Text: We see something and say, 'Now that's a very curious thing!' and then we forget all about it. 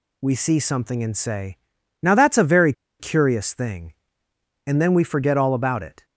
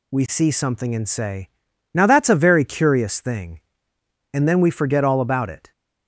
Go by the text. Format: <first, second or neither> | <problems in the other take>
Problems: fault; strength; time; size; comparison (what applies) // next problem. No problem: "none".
second | pauses between "very" and "curious"; slight; at 2.7 s; 0.27 s long